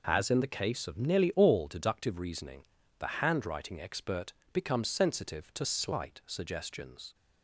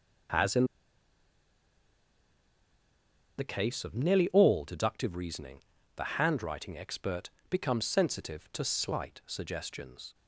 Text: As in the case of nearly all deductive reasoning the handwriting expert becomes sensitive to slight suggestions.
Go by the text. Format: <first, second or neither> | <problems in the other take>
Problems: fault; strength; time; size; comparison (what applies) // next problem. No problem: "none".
first | pauses between "in" and "the"; strong; at 0.6 s; 2.7 s long // pauses between "reasoning" and "the"; slight; at 5.6 s; 0.36 s long; slight in the first // pauses between "expert" and "becomes"; slight; at 7.2 s; 0.22 s long; slight in the first